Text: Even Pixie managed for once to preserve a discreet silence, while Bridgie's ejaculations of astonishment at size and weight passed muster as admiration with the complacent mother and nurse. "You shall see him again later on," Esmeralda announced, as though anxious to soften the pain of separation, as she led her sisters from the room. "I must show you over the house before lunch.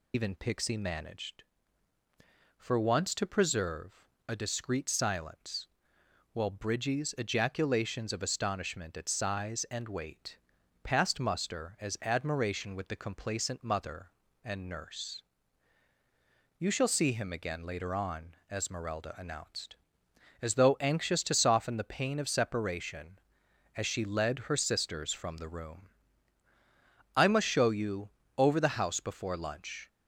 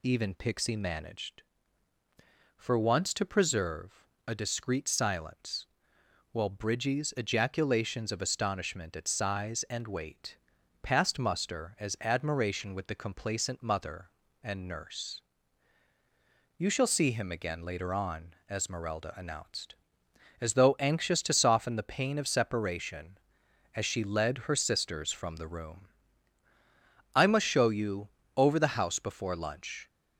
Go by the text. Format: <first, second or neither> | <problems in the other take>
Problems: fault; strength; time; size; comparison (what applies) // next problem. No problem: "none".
second | loses the start of "Even"; at 0.1 s; 105 ms // pauses between "preserve" and "a"; slight; at 4.0 s; 0.22 s long; slight in the second // pauses between "weight" and "passed"; noticeable; at 10.3 s; 0.46 s long; noticeable in the second // pauses between "you" and "over"; slight; at 28.0 s; 0.28 s long; slight in the second